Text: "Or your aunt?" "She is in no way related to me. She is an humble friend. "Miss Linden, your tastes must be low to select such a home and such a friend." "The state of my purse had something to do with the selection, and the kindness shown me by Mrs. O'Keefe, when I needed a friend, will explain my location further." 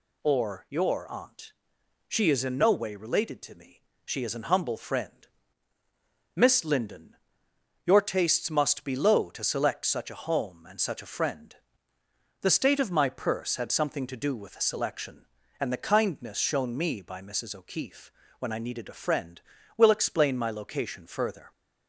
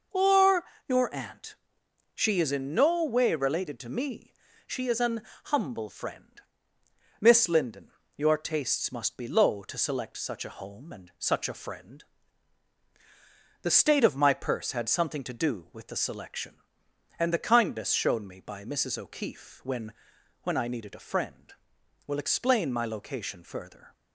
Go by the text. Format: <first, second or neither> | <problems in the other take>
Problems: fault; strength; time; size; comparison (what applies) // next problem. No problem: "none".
first | pauses between "Or" and "your"; slight; at 0.6 s; 0.22 s long // pauses between "an" and "humble"; slight; at 5.2 s; 0.24 s long // says "when" twice; at 20.4 s